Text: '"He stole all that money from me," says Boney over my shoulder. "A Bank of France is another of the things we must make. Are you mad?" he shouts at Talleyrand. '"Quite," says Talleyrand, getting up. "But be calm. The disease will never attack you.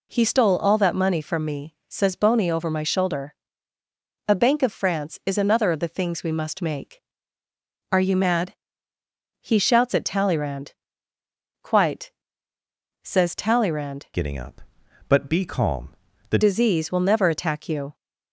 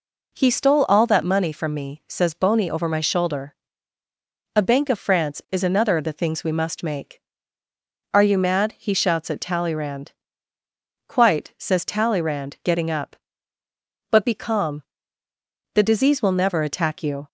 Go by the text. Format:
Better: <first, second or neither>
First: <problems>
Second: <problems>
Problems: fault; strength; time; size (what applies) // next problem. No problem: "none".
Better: second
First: changes voice from "getting" to "The"; from 14.1 to 16.3 s; 2.2 s long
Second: none